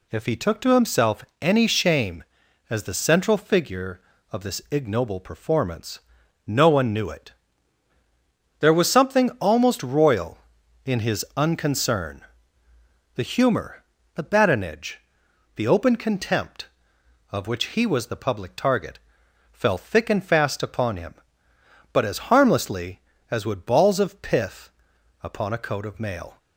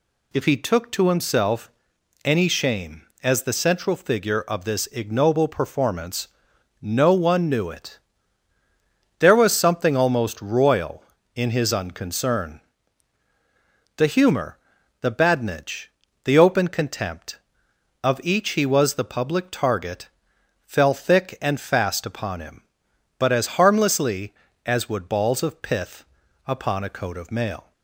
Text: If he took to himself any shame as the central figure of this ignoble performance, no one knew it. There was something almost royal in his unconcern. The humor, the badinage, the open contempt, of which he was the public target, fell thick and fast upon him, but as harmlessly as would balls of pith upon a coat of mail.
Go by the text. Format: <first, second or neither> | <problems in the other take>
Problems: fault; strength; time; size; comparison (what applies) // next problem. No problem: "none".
first | pauses between "himself" and "any"; noticeable; at 1.7 s; 0.54 s long; slight in the first // says "each" for "which"; at 18.2 s // pauses between "pith" and "upon"; at 26.0 s; 0.42 s long; noticeable in the first